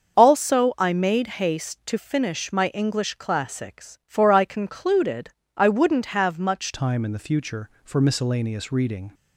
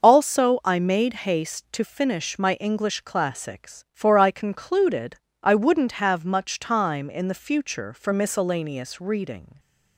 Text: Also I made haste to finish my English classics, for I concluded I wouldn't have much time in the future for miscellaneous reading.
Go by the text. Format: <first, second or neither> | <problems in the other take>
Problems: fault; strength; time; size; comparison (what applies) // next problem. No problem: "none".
second | starts louder than the rest; until 1.2 s; 6.5 dB; also in the second // pauses between "concluded" and "I"; slight; at 5.3 s; 0.26 s long; slight in the second // changes voice at "time"; from 6.7 s on; 2.4 s long